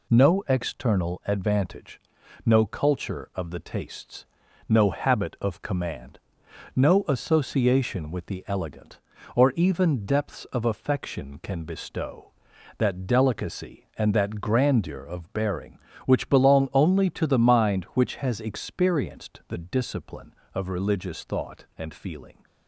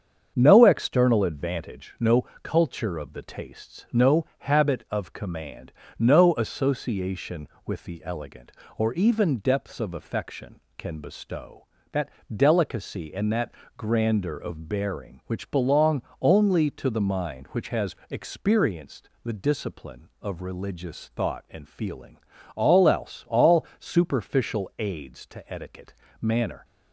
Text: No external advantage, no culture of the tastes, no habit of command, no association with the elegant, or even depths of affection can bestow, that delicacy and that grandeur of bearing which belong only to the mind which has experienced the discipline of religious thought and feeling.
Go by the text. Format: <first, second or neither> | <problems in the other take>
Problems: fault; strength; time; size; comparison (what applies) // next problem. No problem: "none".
first | starts louder than the rest; strong; until 1.3 s; 7 dB // pauses between "no" and "culture"; slight; at 2.2 s; 0.16 s long // pauses between "that" and "delicacy"; slight; at 12.0 s; 0.26 s long // pauses between "that" and "grandeur"; slight; at 13.5 s; 0.24 s long // pauses between "belong" and "only"; slight; at 16.0 s; 0.22 s long // goes on to say "All else all superficial aids to etiquette manner"; strong; from 22.5 s on; 4.0 s long